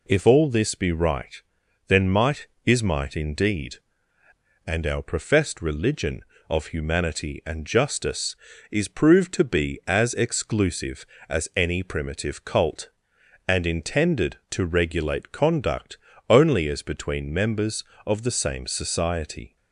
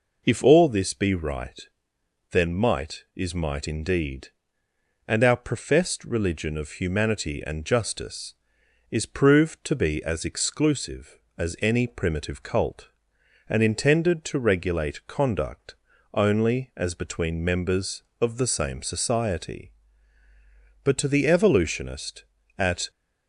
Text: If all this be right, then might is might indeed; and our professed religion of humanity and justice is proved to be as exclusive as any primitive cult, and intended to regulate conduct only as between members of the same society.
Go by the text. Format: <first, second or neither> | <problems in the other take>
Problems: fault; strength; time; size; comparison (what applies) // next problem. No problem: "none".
first | pauses between "conduct" and "only"; at 15.7 s; 0.38 s long; slight in the first // goes on to say "But to the evolutionist at"; strong; from 20.8 s on; 2.0 s long